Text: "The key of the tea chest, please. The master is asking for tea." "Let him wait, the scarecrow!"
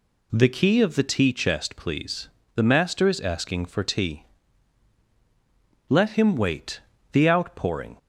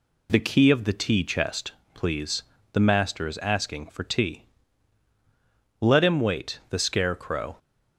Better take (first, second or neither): second